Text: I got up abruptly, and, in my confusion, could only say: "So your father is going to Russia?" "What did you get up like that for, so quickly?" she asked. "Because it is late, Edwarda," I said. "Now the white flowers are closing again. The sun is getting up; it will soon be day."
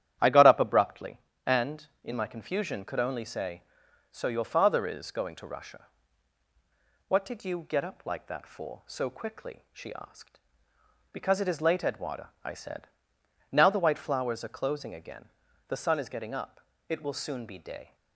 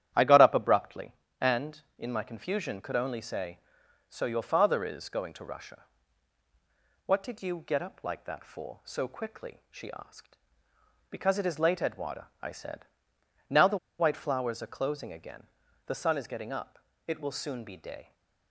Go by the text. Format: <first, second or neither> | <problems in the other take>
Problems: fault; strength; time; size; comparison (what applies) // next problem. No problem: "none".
first | starts louder than the rest; strong; until 1.4 s; 11 dB; strong in the first // pauses between "the" and "white"; slight; at 13.7 s; 0.20 s long